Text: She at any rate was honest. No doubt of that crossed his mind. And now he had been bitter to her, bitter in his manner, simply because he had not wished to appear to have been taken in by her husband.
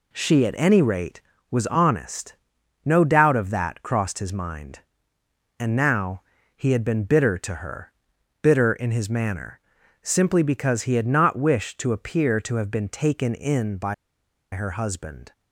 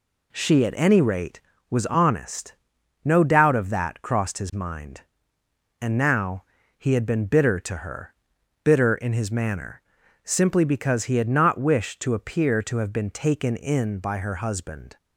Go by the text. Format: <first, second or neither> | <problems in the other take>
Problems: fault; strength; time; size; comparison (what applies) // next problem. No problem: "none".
second | pauses between "now" and "he"; slight; at 6.2 s; 0.32 s long; slight in the second // pauses between "by" and "her"; noticeable; at 13.9 s; 0.59 s long